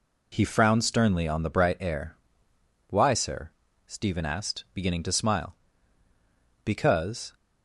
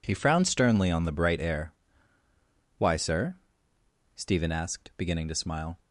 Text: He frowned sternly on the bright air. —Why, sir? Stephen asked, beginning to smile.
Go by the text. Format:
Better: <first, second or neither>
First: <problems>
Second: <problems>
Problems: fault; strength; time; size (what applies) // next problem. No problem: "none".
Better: second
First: goes on to say "Because"; noticeable; from 6.6 s on; 0.70 s long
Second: none